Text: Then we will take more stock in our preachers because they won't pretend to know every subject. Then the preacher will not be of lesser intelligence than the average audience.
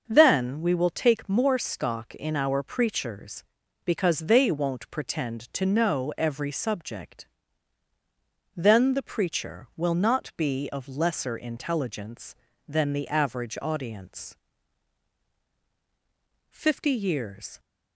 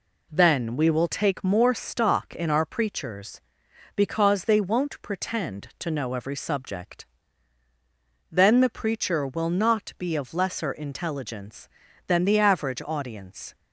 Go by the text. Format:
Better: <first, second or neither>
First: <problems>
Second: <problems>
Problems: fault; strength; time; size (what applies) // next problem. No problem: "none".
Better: second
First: starts louder than the rest; noticeable; until 1.0 s; 6 dB // goes on to say "Fifty years"; noticeable; from 16.5 s on; 1.0 s long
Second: none